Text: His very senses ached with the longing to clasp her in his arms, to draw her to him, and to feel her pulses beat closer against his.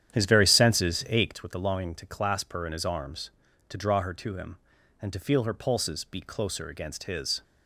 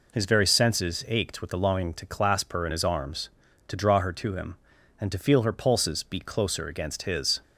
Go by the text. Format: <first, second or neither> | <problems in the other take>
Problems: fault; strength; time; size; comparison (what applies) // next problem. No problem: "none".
second | starts louder than the rest; strong; until 1.3 s; 10 dB